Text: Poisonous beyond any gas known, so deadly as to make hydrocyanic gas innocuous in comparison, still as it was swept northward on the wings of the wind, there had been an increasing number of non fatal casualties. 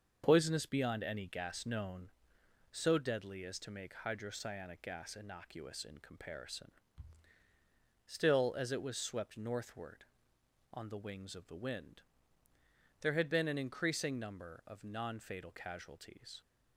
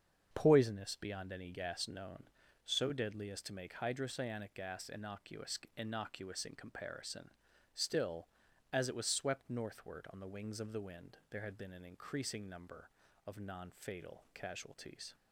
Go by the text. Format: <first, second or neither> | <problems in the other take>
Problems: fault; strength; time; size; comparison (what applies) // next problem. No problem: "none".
first | starts louder than the rest; strong; until 1.3 s; 7 dB; also in the first // says "innocuous" twice; at 5.7 s